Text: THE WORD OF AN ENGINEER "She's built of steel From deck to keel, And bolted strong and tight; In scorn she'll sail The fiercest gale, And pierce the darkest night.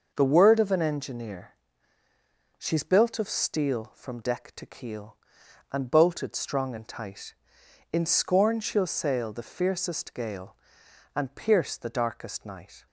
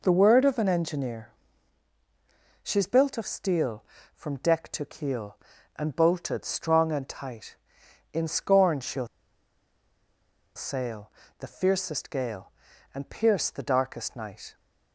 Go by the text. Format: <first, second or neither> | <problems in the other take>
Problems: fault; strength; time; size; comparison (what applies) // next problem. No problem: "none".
first | pauses between "ENGINEER" and "She's"; strong; at 1.2 s; 1.3 s long; also in the first // pauses between "she'll" and "sail"; strong; at 9.0 s; 1.4 s long // pauses between "sail" and "The"; slight; at 11.1 s; 0.28 s long